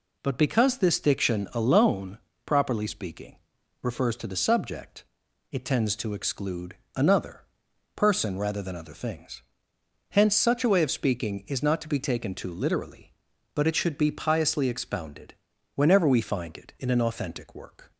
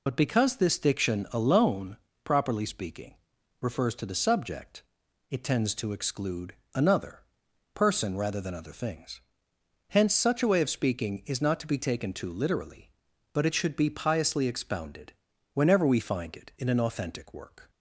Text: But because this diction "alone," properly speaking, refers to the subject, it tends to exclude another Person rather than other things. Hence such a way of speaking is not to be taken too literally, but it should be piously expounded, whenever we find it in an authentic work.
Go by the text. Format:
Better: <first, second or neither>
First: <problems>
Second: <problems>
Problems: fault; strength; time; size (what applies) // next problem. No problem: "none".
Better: first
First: pauses between "exclude" and "another"; slight; at 6.7 s; 0.22 s long // pauses between "another" and "Person"; noticeable; at 7.4 s; 0.54 s long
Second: loses the start of "But"; at 0.0 s; 65 ms // pauses between "exclude" and "another"; slight; at 6.5 s; 0.22 s long // pauses between "another" and "Person"; noticeable; at 7.1 s; 0.54 s long